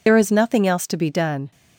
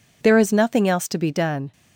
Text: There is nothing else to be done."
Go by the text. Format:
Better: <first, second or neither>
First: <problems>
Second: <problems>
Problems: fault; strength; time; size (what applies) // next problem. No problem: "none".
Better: second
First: loses the start of "There"; at 0.0 s; 65 ms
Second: none